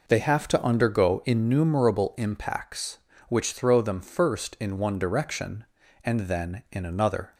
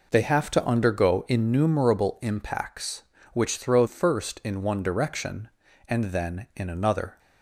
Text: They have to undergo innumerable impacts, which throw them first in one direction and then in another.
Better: first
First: none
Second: skips "them"; at 3.8 s

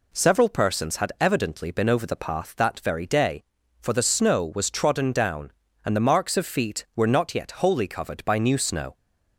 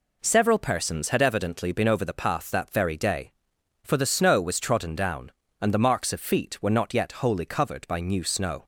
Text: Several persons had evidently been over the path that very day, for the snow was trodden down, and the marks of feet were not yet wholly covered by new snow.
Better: neither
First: none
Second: none

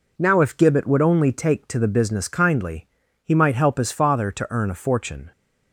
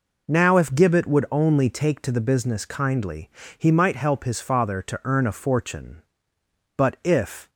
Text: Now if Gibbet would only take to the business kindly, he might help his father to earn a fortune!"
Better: first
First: none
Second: goes on to say "But if"; noticeable; from 6.7 s on; 0.72 s long

